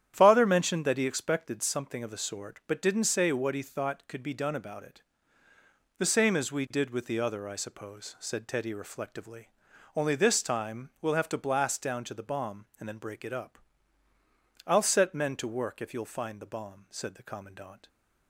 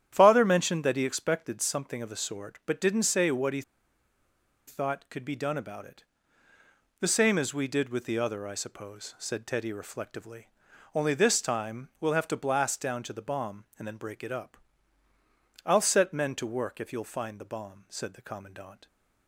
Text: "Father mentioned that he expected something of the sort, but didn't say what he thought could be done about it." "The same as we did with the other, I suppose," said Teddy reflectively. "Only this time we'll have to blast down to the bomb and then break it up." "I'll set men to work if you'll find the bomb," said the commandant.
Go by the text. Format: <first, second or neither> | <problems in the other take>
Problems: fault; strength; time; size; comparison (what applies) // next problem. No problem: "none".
first | starts louder than the rest; strong; until 1.1 s; 10.5 dB; strong in the first // pauses between "he" and "thought"; at 3.6 s; 1.0 s long